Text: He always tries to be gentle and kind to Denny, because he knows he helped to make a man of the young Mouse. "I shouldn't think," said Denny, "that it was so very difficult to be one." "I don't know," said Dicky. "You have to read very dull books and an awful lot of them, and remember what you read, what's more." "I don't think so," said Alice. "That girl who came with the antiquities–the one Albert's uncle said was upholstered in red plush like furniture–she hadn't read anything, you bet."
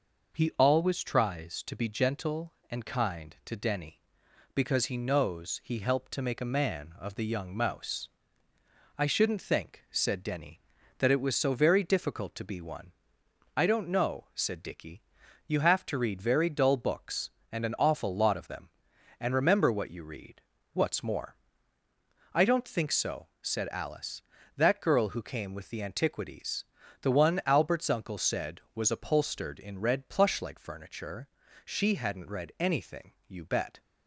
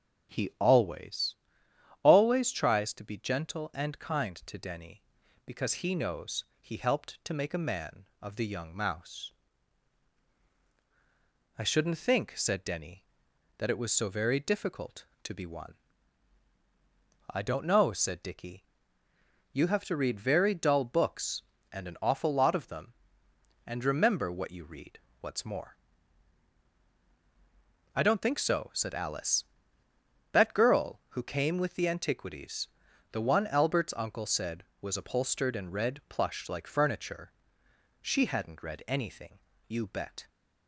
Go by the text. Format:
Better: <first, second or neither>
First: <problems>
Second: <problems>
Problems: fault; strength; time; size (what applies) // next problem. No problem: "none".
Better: first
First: none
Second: starts louder than the rest; strong; until 2.0 s; 7.5 dB // says "always" twice; at 2.0 s // pauses between "knows" and "he"; slight; at 6.4 s; 0.16 s long